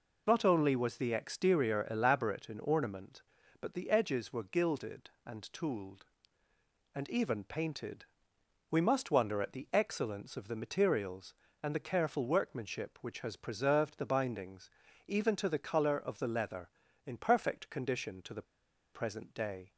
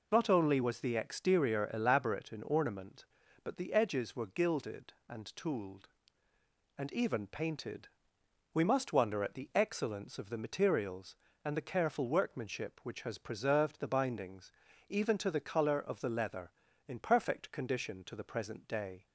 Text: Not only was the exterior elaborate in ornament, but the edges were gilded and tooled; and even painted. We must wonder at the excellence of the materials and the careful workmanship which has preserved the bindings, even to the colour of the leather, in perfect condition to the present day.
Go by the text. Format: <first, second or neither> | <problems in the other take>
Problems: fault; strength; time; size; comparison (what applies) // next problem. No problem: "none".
second | pauses between "the" and "present"; noticeable; at 18.4 s; 0.51 s long